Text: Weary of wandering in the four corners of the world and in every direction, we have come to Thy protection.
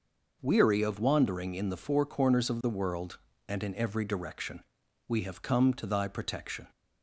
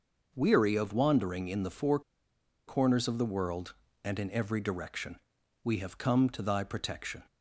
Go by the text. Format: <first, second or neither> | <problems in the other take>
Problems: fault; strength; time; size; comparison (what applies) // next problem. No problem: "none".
first | pauses between "four" and "corners"; noticeable; at 1.9 s; 0.67 s long